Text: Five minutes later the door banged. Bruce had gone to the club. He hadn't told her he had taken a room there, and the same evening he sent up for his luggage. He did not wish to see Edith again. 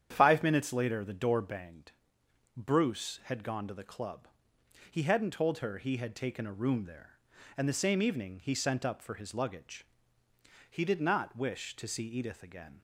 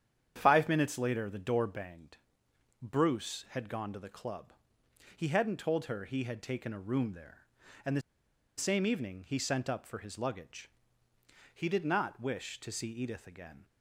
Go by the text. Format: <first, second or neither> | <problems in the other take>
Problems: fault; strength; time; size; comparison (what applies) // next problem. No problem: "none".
first | starts louder than the rest; strong; until 1.3 s; 9 dB; strong in the first // pauses between "the" and "same"; noticeable; at 8.0 s; 0.57 s long